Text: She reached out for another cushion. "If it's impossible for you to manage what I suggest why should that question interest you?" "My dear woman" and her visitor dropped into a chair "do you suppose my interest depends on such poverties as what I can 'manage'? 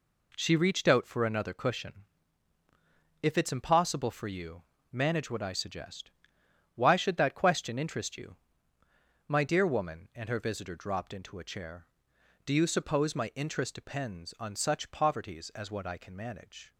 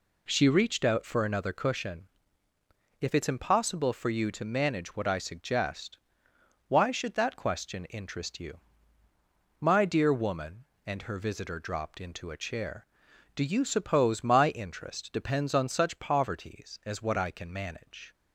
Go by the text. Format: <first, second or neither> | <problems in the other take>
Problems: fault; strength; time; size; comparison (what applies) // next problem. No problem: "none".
second | skips "to"; at 4.7 s // pauses between "suggest" and "why"; noticeable; at 6.0 s; 0.64 s long; noticeable in the second